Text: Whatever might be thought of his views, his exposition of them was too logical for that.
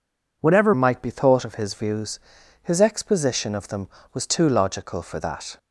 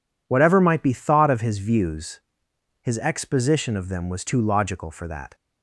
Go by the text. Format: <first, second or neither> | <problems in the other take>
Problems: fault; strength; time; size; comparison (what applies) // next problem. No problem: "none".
second | changes voice at "might"; from 0.7 s on; 4.8 s long